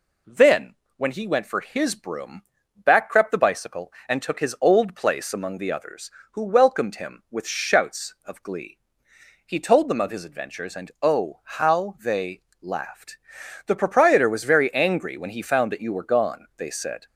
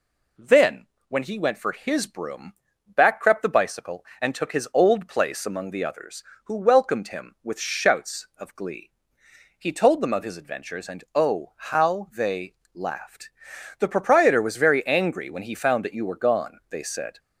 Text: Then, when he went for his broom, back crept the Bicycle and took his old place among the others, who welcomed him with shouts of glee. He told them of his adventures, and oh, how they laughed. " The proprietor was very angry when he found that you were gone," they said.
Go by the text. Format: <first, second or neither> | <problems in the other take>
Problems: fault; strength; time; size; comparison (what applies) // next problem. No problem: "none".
neither | pauses between "they" and "laughed"; slight; the same in both